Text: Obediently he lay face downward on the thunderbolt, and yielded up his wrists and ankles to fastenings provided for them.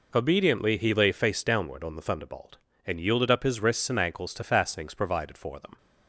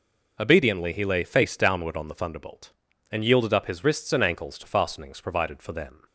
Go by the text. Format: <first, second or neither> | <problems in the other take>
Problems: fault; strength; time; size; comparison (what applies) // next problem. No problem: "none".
neither | none